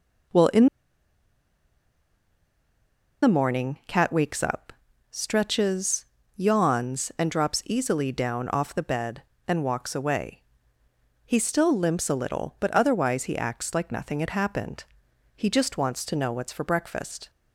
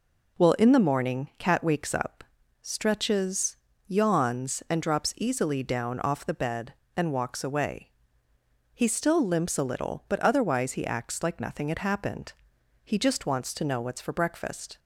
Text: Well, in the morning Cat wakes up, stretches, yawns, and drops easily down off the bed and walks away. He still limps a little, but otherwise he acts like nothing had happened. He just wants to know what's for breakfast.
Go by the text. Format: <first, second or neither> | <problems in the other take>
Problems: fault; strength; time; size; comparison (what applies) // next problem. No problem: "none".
second | pauses between "in" and "the"; strong; at 0.6 s; 2.5 s long